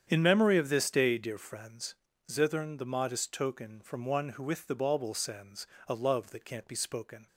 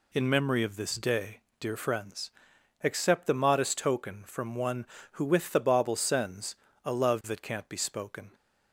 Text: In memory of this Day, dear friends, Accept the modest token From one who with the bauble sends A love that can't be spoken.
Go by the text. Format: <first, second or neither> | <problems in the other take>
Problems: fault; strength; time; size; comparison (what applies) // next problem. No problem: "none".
second | starts louder than the rest; strong; until 1.1 s; 8.5 dB // says "Zithern" for "Accept"; at 2.3 s // pauses between "sends" and "A"; slight; at 5.6 s; 0.22 s long; slight in the second